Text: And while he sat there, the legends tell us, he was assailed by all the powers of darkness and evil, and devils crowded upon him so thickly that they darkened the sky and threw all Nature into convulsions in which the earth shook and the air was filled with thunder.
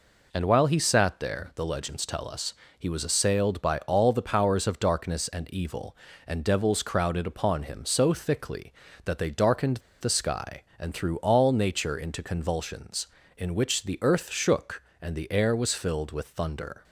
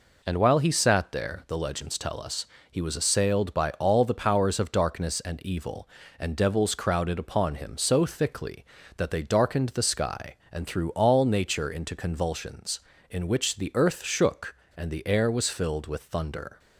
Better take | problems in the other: second | pauses between "darkened" and "the"; slight; at 9.7 s; 0.22 s long

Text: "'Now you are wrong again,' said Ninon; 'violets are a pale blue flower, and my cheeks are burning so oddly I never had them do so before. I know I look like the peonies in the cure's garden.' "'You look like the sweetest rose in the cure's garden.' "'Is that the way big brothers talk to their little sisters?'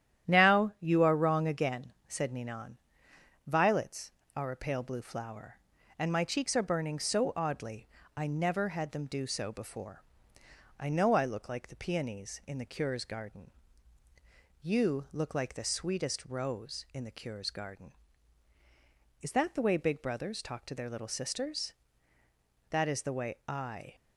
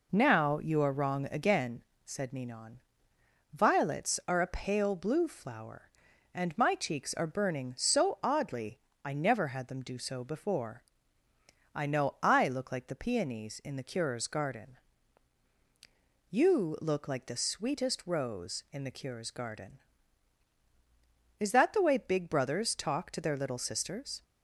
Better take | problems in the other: second | starts louder than the rest; strong; until 1.3 s; 11 dB // pauses between "oddly" and "I"; slight; at 7.8 s; 0.30 s long; slight in the second // goes on to say "That is the way I"; noticeable; from 22.7 s on; 1.2 s long

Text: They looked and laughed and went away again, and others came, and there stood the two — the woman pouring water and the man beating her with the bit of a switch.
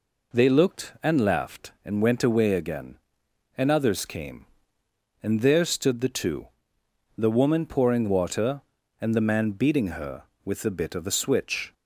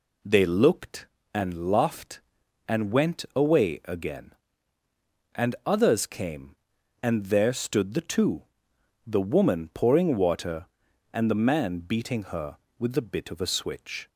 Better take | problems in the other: neither | none

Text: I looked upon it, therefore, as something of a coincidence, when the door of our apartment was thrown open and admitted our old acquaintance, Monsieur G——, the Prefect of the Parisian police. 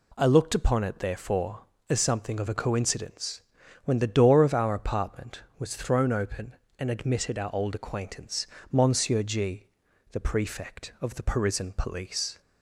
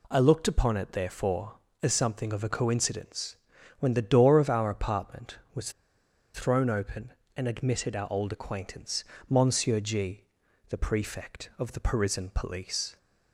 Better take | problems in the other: first | pauses between "was" and "thrown"; noticeable; at 5.7 s; 0.62 s long

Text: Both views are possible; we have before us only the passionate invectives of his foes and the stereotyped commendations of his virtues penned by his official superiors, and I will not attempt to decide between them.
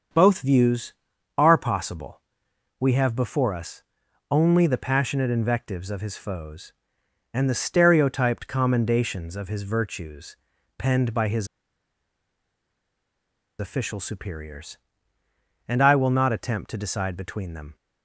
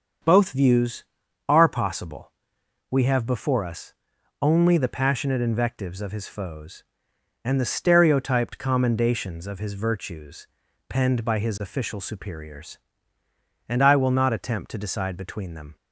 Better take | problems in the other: second | starts louder than the rest; until 1.5 s; 7 dB; also in the second // pauses between "us" and "only"; noticeable; at 3.8 s; 0.48 s long; noticeable in the second // pauses between "virtues" and "penned"; at 10.3 s; 0.42 s long; also in the second // pauses between "his" and "official"; strong; at 11.4 s; 2.1 s long

